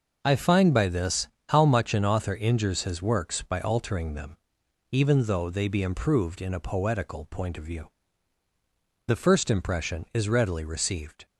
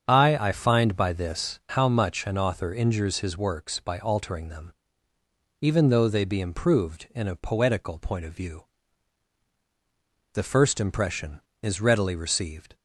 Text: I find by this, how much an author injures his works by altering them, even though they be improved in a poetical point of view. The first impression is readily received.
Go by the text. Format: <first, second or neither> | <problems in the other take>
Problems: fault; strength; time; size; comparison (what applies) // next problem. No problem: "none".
first | starts louder than the rest; strong; until 1.0 s; 7.5 dB // says "I" twice; at 0.3 s